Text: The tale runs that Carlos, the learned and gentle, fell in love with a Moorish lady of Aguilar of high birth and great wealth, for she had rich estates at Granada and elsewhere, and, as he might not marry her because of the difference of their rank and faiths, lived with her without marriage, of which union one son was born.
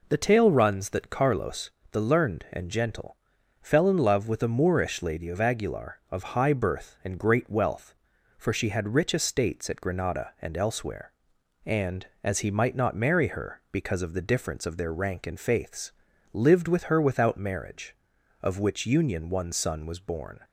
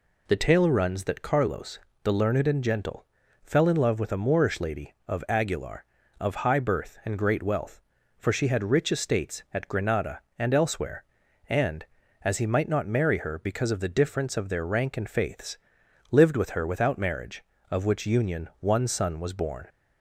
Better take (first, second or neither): neither